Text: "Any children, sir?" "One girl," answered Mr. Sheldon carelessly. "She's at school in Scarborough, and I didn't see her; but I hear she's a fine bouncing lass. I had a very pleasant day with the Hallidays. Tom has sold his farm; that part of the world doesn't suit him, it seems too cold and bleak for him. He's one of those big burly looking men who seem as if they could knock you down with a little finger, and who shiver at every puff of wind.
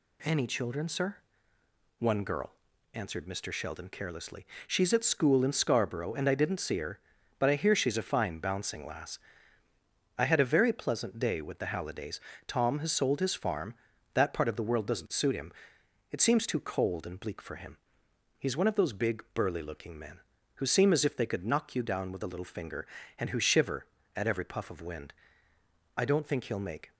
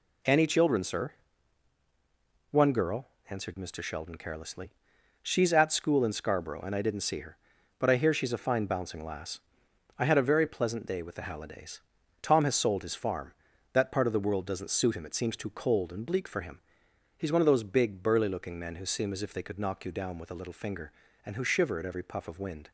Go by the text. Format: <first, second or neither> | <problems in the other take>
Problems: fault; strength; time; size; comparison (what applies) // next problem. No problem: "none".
second | goes on to say "I don't think he'll make"; noticeable; from 25.9 s on; 0.96 s long